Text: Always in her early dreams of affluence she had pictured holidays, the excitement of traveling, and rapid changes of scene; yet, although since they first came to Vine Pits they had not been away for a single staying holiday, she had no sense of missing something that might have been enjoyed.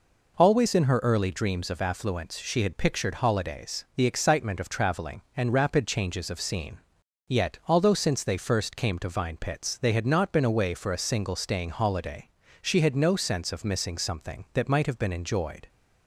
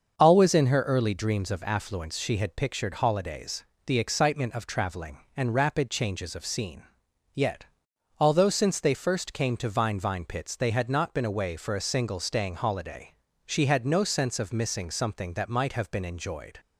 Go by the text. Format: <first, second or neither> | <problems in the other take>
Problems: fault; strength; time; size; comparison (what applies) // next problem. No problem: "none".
first | starts louder than the rest; until 1.2 s; 6.5 dB // says "Vine" twice; at 9.9 s